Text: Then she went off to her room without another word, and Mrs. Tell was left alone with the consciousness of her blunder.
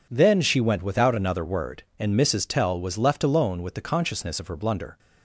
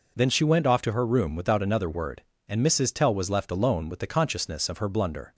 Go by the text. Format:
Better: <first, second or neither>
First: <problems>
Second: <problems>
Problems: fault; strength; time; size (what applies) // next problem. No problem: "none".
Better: second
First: skips "off to her room"; at 0.8 s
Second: none